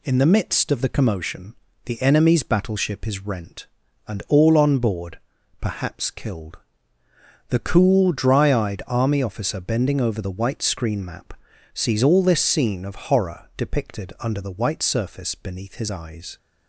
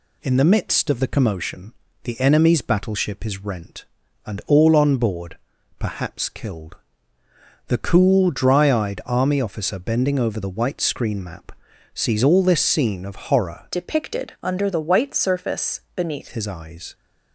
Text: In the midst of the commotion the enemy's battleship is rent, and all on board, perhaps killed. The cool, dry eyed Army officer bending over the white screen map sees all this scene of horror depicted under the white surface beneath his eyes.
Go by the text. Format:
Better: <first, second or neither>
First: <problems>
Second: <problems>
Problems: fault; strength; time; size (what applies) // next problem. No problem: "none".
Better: first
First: pauses between "commotion" and "the"; slight; at 1.5 s; 0.30 s long // pauses between "map" and "sees"; at 11.3 s; 0.38 s long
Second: pauses between "commotion" and "the"; slight; at 1.7 s; 0.30 s long // pauses between "map" and "sees"; at 11.5 s; 0.40 s long // changes voice from "depicted" to "beneath"; from 13.7 to 16.2 s; 2.5 s long // pauses between "surface" and "beneath"; slight; at 15.8 s; 0.16 s long